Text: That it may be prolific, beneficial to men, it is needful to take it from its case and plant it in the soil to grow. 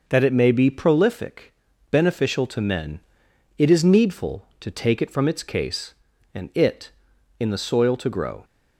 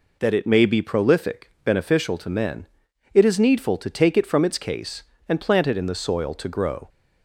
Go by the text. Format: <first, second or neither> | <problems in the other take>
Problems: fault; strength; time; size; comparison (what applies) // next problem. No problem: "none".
second | skips "plant"; at 6.5 s